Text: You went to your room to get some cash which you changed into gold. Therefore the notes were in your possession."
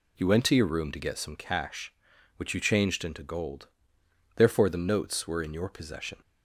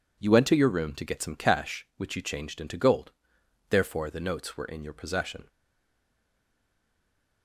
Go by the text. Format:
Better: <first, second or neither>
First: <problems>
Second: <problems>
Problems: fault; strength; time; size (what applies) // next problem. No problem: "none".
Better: first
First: none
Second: stays silent after the last word; noticeable; from 5.4 s on; 2.0 s long